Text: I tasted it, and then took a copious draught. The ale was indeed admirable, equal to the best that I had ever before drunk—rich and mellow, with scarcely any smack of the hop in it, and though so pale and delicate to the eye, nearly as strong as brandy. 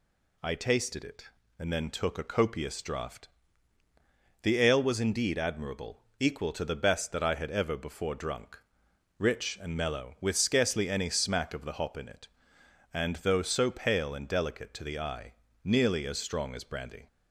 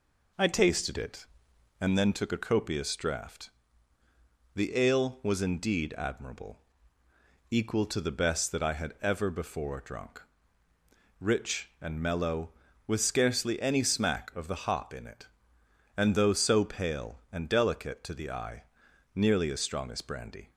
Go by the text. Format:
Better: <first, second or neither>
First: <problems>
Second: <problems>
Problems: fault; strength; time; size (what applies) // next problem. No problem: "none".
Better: first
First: none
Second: starts louder than the rest; noticeable; until 2.1 s; 4 dB